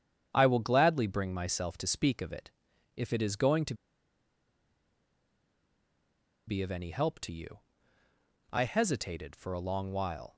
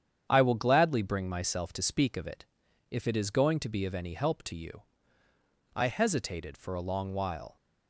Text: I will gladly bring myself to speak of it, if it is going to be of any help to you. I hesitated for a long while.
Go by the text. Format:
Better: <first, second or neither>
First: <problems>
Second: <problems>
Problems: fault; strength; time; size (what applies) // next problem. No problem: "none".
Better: second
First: starts louder than the rest; strong; until 1.3 s; 8.5 dB // pauses between "to" and "be"; strong; at 3.7 s; 2.7 s long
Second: starts louder than the rest; strong; until 1.2 s; 8.5 dB